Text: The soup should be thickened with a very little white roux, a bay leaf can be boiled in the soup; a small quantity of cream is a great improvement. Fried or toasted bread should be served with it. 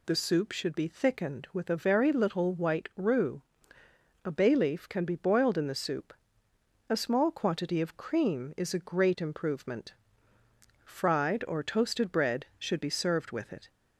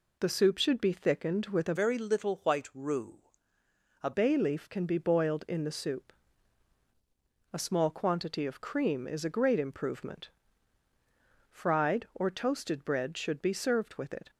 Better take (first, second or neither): first